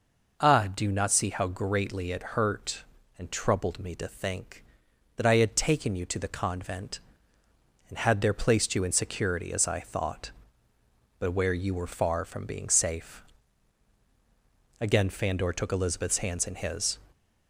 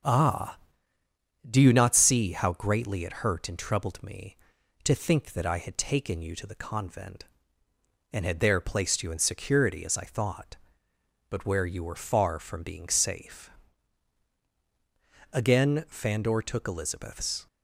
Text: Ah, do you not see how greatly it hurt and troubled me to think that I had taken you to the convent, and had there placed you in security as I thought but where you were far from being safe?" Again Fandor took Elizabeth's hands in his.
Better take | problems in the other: first | starts louder than the rest; noticeable; until 1.9 s; 6 dB // stops before "hands in his"; at 17.4 s

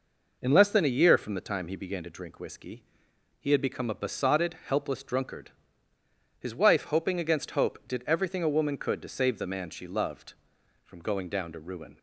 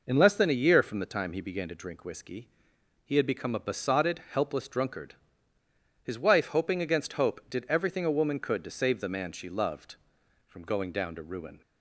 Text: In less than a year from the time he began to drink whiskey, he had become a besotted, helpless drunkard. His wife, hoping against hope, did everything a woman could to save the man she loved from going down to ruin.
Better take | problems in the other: neither | none

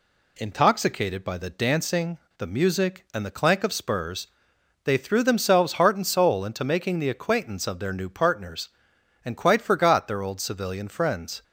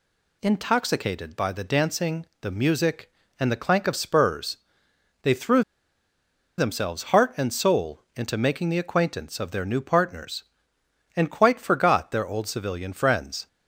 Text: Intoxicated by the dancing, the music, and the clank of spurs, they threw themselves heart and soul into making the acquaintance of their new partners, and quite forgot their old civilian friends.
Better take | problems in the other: first | pauses between "threw" and "themselves"; noticeable; at 5.6 s; 0.97 s long

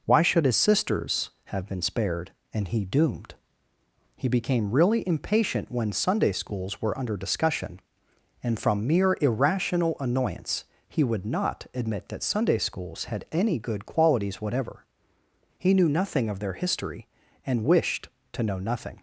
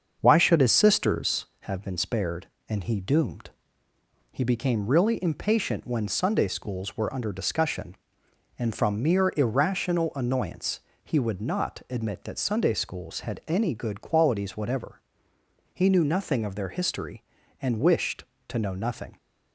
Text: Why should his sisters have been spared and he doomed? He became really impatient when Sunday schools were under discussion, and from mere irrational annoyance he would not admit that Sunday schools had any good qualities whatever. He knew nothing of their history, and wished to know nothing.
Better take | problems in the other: first | starts louder than the rest; until 1.5 s; 7 dB // pauses between "annoyance" and "he"; slight; at 10.8 s; 0.22 s long; slight in the first

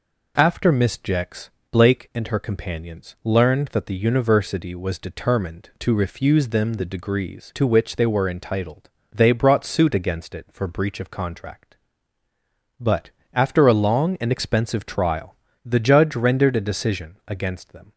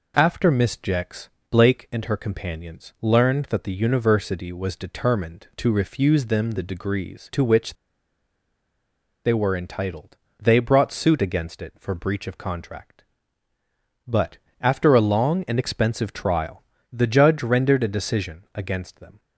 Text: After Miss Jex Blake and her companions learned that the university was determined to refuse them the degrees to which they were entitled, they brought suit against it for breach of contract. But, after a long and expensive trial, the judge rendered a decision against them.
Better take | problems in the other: first | pauses between "Jex" and "Blake"; slight; at 1.2 s; 0.22 s long; slight in the first // pauses between "which" and "they"; strong; at 7.7 s; 1.5 s long

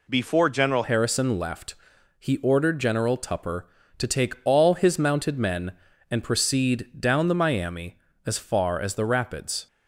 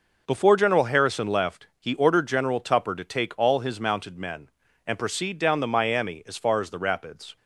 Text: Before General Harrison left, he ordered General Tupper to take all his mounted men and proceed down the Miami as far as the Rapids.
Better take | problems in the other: second | changes voice at "Harrison"; from 0.8 s on; 8.8 s long

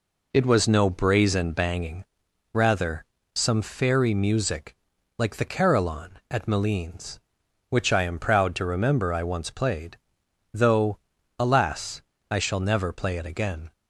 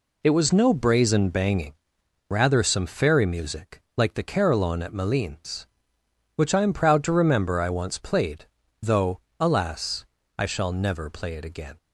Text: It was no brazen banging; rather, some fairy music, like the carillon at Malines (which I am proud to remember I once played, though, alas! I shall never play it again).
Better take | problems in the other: neither | none

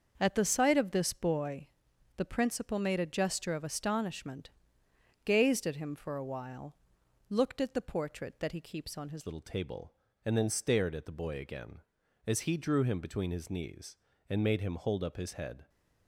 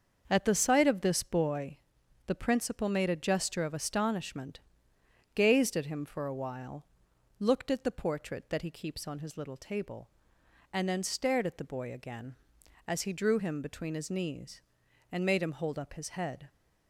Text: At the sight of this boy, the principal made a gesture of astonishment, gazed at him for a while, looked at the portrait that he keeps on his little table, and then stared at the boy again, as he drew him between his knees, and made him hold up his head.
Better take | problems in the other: second | starts louder than the rest; until 1.1 s; 6.5 dB; also in the second // changes voice at "little"; from 9.2 s on; 6.4 s long

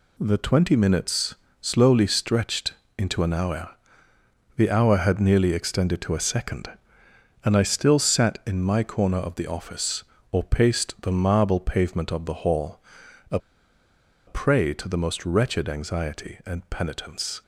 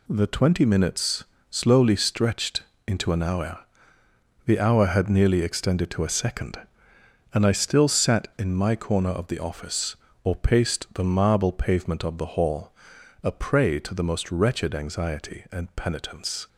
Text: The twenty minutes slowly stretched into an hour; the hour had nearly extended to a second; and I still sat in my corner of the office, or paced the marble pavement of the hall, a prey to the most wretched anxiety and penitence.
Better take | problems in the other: second | pauses between "minutes" and "slowly"; slight; at 1.3 s; 0.26 s long; slight in the second // pauses between "stretched" and "into"; slight; at 2.7 s; 0.24 s long; slight in the second // pauses between "a" and "prey"; noticeable; at 13.3 s; 0.89 s long

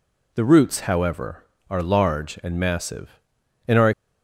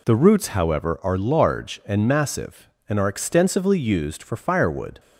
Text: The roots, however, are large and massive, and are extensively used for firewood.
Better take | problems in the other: second | stops before "extensively used for firewood"; at 3.9 s

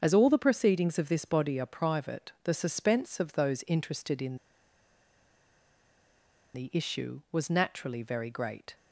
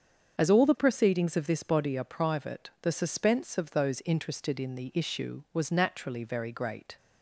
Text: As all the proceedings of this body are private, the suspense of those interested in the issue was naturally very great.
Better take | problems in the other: second | starts louder than the rest; strong; until 1.0 s; 7 dB; strong in the second // pauses between "in" and "the"; strong; at 4.3 s; 2.1 s long

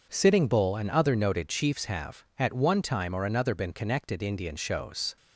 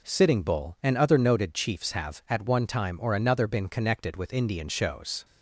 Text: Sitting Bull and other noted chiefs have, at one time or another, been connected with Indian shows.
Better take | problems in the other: second | skips "with"; at 4.2 s

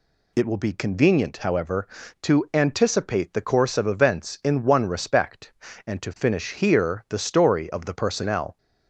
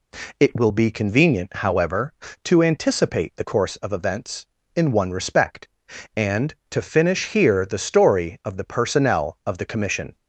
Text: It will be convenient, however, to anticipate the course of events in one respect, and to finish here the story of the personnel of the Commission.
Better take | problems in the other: second | stops before "of the Commission"; at 8.5 s

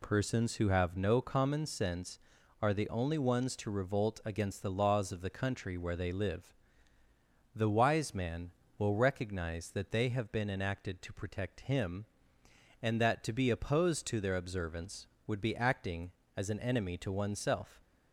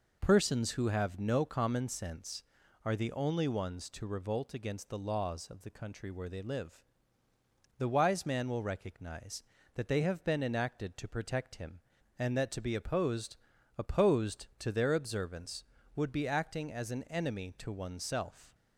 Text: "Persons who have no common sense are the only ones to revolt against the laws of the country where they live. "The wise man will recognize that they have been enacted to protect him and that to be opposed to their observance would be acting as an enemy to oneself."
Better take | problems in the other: first | says "opposed" twice; at 13.7 s

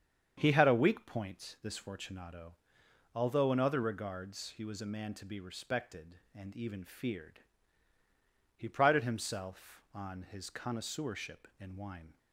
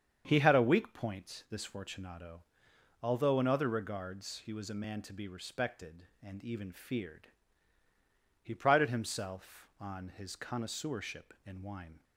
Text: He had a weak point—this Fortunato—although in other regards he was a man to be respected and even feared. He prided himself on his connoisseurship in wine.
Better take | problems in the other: neither | starts louder than the rest; strong; the same in both

